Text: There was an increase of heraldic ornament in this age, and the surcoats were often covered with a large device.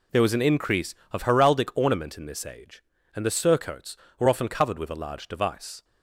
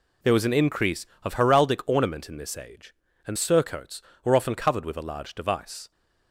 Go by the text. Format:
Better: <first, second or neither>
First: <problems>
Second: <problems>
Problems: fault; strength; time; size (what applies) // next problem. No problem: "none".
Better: first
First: none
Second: skips "the"; at 3.3 s